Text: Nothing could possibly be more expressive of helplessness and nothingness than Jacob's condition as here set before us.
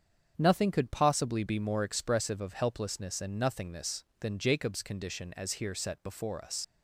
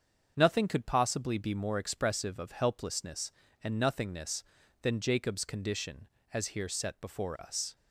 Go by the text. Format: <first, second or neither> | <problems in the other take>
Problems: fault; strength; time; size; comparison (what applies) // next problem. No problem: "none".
second | starts louder than the rest; strong; until 1.3 s; 7.5 dB; also in the second // leaves "us" unfinished; at 6.6 s; 75 ms